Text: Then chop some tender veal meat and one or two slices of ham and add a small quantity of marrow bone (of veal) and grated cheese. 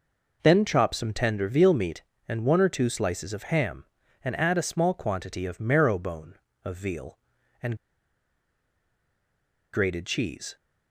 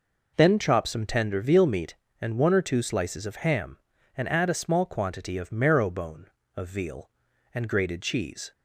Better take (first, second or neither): second